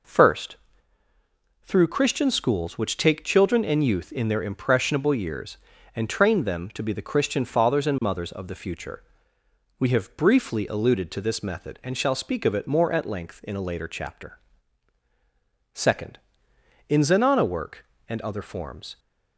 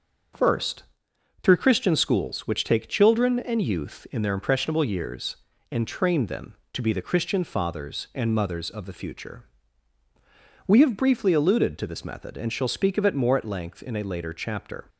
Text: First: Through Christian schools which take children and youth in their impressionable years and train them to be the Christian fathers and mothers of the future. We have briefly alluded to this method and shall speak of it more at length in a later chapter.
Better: second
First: goes on to say "Second In Zenana work and other forms"; strong; from 15.7 s on; 3.2 s long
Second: none

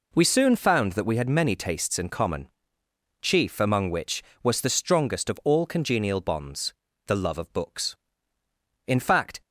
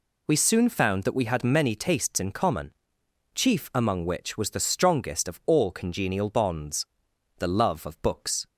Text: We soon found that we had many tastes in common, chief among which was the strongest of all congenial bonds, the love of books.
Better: second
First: goes on to say "In fact"; from 8.8 s on; 0.54 s long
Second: none

